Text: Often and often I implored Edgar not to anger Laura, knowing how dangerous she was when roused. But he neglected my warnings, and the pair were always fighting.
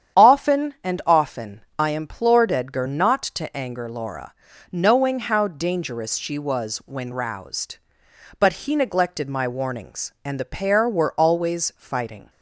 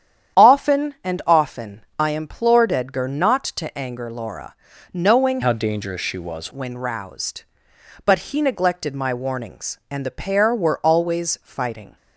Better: first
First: starts louder than the rest; strong; until 1.3 s; 9 dB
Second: starts louder than the rest; strong; until 1.5 s; 9.5 dB // changes voice from "how" to "was"; from 5.4 to 6.5 s; 1.1 s long

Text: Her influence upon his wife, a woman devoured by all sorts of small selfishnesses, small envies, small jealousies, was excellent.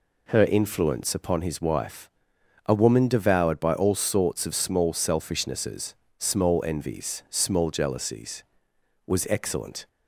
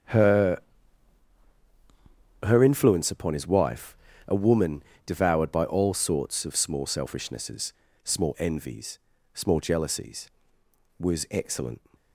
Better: first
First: none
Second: starts louder than the rest; strong; until 2.9 s; 8.5 dB // says "Her" twice; at 2.4 s // pauses between "woman" and "devoured"; slight; at 4.8 s; 0.22 s long

